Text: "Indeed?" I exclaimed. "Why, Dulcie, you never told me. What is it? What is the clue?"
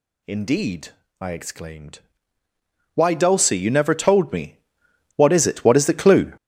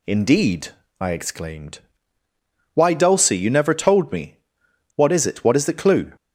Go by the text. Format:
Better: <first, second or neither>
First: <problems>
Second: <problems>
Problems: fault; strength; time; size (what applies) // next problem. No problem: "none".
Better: second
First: gets louder; strong; throughout; 13 dB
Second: none